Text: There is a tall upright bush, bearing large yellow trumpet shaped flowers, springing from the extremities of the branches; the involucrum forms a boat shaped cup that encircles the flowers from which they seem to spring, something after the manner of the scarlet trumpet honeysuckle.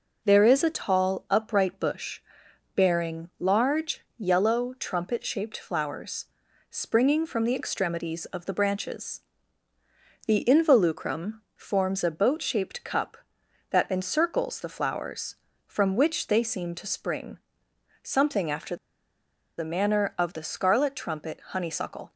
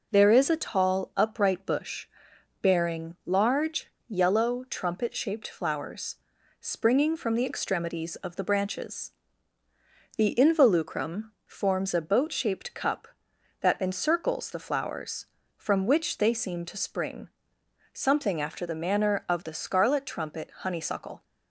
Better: second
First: pauses between "large" and "yellow"; slight; at 4.0 s; 0.16 s long // pauses between "involucrum" and "forms"; slight; at 11.4 s; 0.16 s long // pauses between "after" and "the"; noticeable; at 18.7 s; 0.81 s long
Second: pauses between "large" and "yellow"; slight; at 3.8 s; 0.20 s long // pauses between "involucrum" and "forms"; slight; at 11.3 s; 0.16 s long

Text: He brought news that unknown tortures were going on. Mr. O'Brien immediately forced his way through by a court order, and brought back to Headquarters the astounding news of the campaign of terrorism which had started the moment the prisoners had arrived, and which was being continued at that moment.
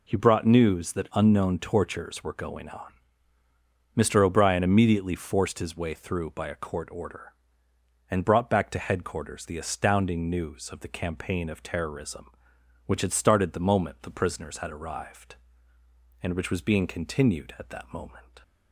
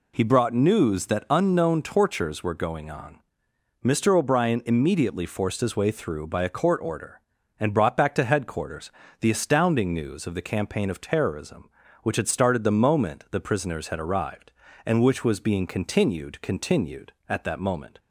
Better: first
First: none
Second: pauses between "Headquarters" and "the"; slight; at 8.9 s; 0.26 s long // says "continued" twice; at 16.4 s

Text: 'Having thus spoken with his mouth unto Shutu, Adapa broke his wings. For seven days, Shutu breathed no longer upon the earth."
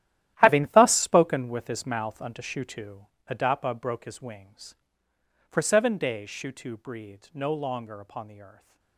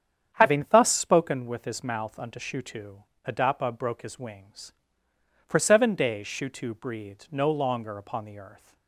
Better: second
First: gets quieter; strong; throughout; 14.5 dB // starts louder than the rest; strong; until 1.4 s; 13 dB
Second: starts louder than the rest; strong; until 1.3 s; 8.5 dB

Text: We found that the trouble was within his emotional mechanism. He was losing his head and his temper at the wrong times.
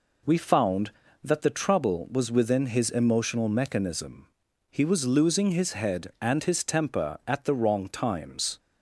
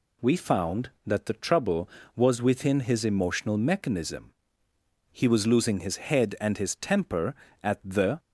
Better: first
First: none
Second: stops before "wrong times"; at 8.1 s

